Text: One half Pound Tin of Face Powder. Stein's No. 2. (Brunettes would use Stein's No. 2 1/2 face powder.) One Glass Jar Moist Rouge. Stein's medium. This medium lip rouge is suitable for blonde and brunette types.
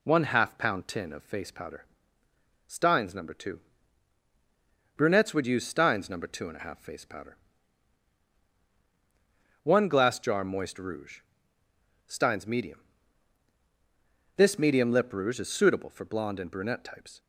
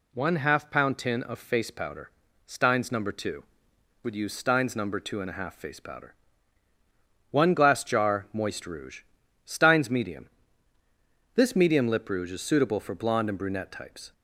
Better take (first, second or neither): first